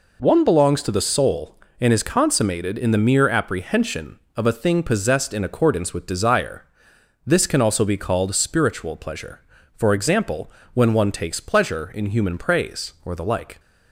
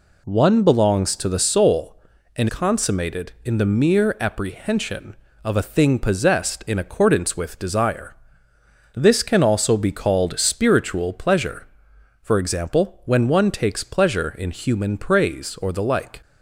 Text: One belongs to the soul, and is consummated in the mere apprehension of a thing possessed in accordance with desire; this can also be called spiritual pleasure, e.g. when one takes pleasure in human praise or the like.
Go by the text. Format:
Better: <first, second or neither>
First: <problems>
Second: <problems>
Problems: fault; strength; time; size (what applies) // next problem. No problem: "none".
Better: first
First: none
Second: skips "is"; at 2.4 s